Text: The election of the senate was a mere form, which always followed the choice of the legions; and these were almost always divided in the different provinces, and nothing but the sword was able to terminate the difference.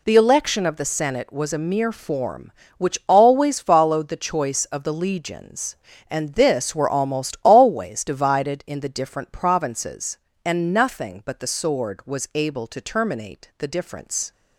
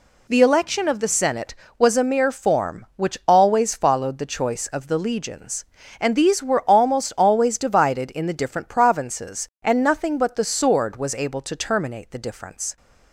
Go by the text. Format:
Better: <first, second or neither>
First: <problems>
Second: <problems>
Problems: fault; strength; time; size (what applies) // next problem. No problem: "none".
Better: second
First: says "this" for "these"; at 6.3 s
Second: none